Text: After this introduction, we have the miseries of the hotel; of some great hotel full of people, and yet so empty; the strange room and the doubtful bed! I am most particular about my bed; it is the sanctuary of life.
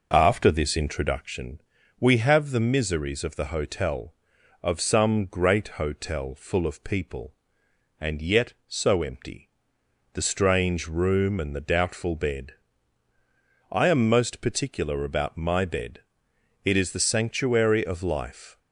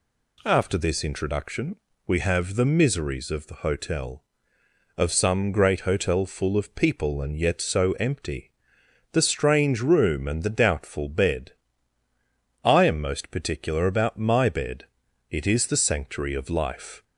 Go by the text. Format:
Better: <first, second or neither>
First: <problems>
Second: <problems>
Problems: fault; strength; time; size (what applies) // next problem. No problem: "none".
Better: second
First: starts louder than the rest; noticeable; until 1.3 s; 5.5 dB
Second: none